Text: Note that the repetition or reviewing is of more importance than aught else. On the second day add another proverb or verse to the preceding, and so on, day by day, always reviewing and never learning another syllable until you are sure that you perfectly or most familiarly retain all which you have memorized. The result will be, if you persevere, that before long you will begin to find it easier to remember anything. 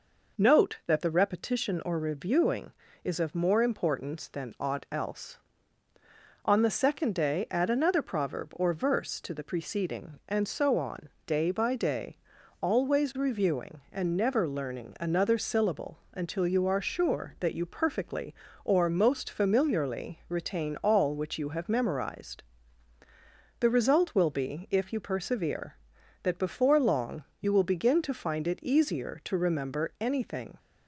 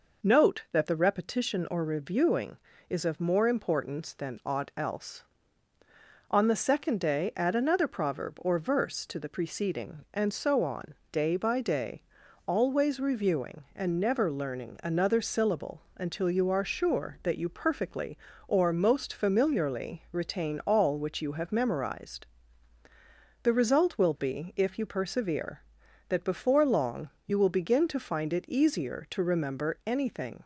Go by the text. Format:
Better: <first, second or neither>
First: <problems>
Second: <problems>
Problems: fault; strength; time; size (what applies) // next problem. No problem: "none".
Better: neither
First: pauses between "long" and "you"; slight; at 27.2 s; 0.16 s long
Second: pauses between "long" and "you"; slight; at 27.0 s; 0.16 s long